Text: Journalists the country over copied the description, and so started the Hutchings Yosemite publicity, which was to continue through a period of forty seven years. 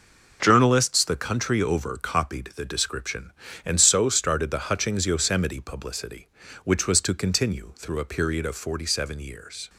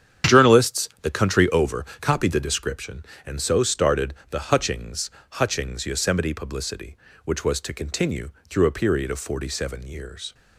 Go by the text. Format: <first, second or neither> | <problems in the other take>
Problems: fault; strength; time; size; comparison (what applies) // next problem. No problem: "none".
first | starts louder than the rest; strong; until 1.4 s; 8.5 dB // pauses between "started" and "the"; slight; at 4.1 s; 0.16 s long // says "Hutchings" twice; at 5.3 s // pauses between "continue" and "through"; slight; at 8.2 s; 0.18 s long